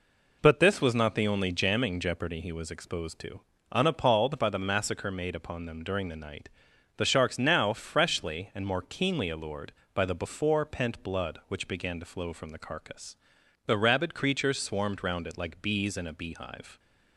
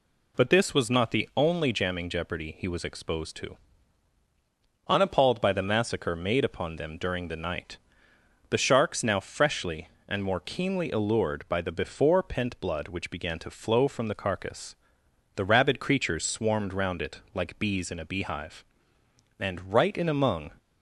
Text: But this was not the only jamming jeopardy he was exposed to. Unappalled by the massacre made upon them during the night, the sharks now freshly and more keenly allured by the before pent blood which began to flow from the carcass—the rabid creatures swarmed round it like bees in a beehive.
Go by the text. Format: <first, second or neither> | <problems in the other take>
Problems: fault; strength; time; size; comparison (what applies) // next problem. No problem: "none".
first | goes on to say "And right in among"; noticeable; from 19.3 s on; 1.1 s long